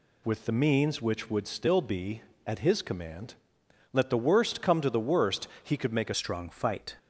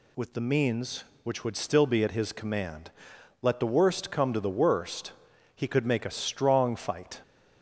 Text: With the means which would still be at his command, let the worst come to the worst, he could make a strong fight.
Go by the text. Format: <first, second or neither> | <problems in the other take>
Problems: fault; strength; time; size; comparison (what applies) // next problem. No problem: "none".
second | changes voice at "strong"; from 6.1 s on; 0.8 s long